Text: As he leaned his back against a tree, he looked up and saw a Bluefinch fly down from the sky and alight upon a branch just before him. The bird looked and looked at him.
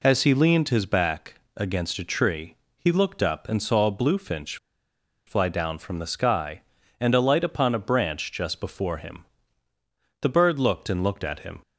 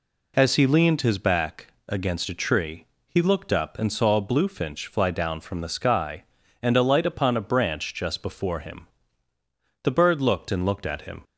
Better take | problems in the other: second | pauses between "back" and "against"; slight; at 1.3 s; 0.18 s long; slight in the second // pauses between "Bluefinch" and "fly"; noticeable; at 4.5 s; 0.70 s long

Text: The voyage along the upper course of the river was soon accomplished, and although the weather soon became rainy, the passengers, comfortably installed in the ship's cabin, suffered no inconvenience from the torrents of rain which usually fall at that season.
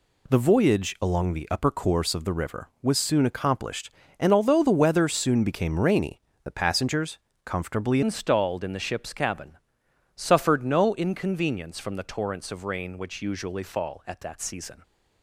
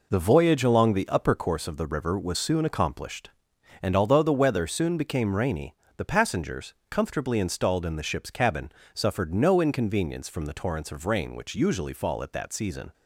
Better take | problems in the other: second | changes voice at "installed"; from 8.0 s on; 6.8 s long

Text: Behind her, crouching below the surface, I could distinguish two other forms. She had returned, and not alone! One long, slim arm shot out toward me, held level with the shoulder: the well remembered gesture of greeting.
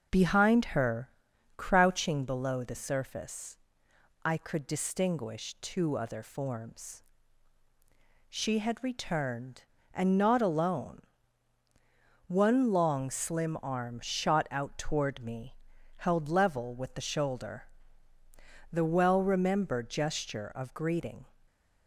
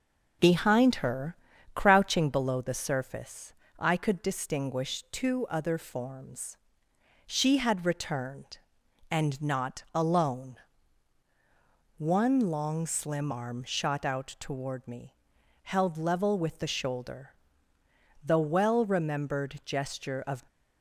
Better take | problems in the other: first | stops before "greeting"; at 20.4 s

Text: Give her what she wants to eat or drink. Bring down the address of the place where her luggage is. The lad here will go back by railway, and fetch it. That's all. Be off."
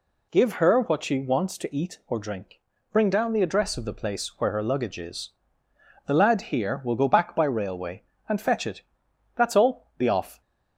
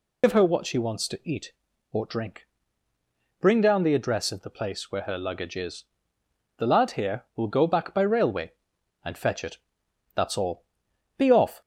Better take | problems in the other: first | loses the start of "Give"; at 0.2 s; 80 ms

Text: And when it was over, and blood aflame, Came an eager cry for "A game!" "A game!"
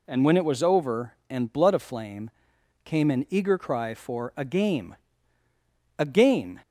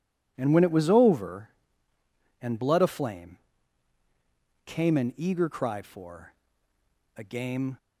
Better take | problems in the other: first | pauses between "for" and "A"; noticeable; at 6.3 s; 0.86 s long // stops before "A game"; at 7.7 s

